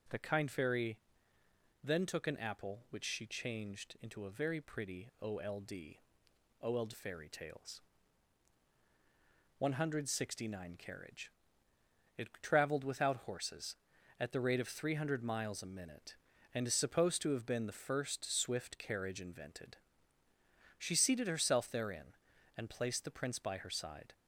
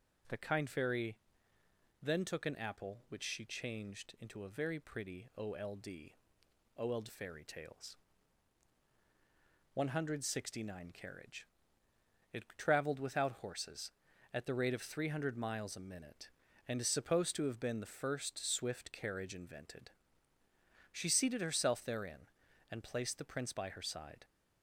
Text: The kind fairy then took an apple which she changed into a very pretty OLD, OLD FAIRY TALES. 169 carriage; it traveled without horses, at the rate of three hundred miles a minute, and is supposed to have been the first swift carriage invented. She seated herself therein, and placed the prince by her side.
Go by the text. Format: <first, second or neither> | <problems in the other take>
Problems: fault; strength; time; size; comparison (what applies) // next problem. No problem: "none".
neither | pauses between "fairy" and "then"; noticeable; the same in both